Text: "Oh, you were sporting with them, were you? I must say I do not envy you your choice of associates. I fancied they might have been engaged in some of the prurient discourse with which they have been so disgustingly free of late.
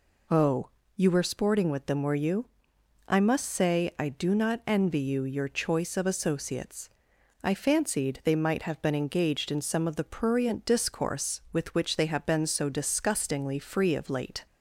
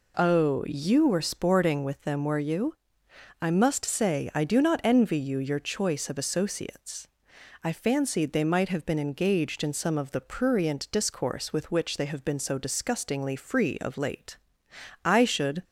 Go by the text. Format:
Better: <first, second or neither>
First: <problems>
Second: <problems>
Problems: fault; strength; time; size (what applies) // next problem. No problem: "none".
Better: first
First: none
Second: goes on to say "I should"; from 15.0 s on; 0.60 s long